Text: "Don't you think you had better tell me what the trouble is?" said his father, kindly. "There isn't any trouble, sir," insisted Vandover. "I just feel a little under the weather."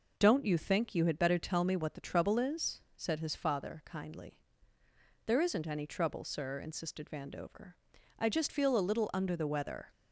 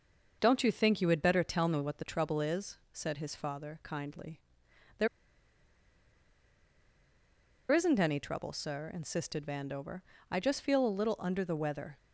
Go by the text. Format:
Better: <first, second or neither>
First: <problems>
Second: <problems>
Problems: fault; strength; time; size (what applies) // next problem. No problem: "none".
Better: first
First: none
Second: starts louder than the rest; until 1.4 s; 6.5 dB // pauses between "There" and "isn't"; strong; at 5.0 s; 2.6 s long